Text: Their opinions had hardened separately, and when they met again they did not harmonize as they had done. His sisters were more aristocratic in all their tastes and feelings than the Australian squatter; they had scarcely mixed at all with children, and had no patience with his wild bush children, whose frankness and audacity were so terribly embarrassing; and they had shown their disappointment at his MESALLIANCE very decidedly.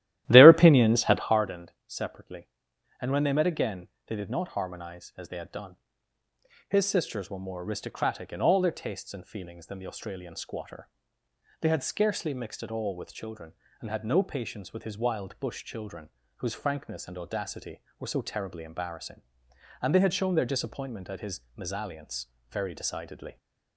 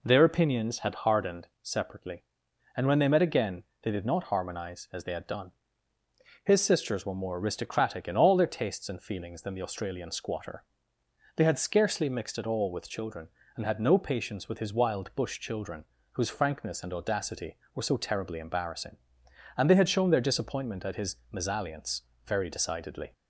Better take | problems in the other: second | starts louder than the rest; strong; until 1.4 s; 13.5 dB // pauses between "again" and "they"; slight; at 3.8 s; 0.18 s long; slight in the second // pauses between "MESALLIANCE" and "very"; slight; at 22.2 s; 0.20 s long; slight in the second

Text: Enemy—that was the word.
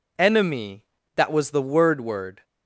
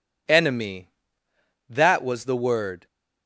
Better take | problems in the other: second | says "word" twice; at 1.9 s

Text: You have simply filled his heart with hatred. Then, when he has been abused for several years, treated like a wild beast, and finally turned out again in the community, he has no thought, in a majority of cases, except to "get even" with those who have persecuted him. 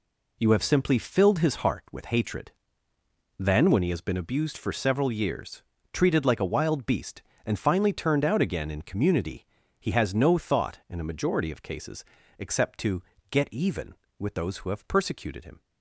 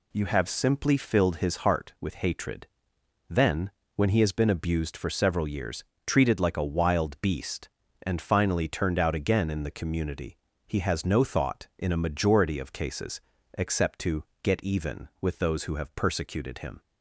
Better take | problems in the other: second | skips "the"; at 8.8 s // pauses between "to" and "get"; slight; at 13.0 s; 0.28 s long; slight in the second

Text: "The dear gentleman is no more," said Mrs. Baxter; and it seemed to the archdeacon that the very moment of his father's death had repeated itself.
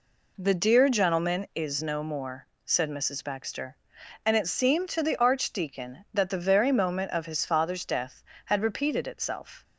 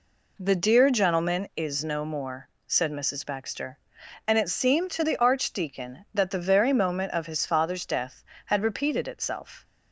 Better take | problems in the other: neither | none

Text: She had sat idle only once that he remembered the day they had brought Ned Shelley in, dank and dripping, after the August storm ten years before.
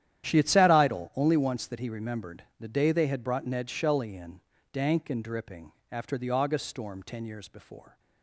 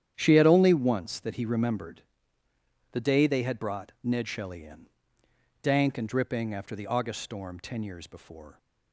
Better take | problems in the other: first | starts louder than the rest; strong; until 1.1 s; 10 dB; strong in the first // skips "sat idle"; at 0.4 s // pauses between "remembered" and "the"; noticeable; at 2.0 s; 0.90 s long

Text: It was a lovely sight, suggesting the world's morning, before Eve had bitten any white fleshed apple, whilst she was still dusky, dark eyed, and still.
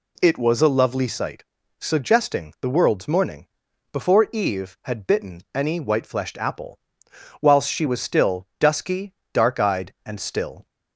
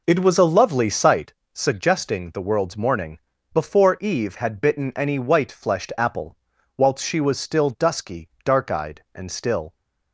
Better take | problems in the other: first | starts louder than the rest; noticeable; until 1.4 s; 4.5 dB

